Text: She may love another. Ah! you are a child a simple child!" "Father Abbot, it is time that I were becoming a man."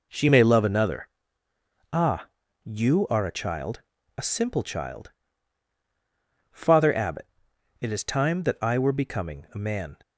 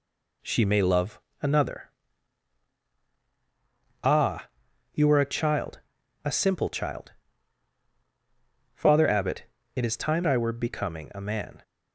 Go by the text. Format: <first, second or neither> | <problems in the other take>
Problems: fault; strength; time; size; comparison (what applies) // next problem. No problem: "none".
first | pauses between "love" and "another"; slight; at 1.1 s; 0.22 s long // pauses between "child" and "a"; at 5.8 s; 0.42 s long; slight in the first // skips "that"; at 10.2 s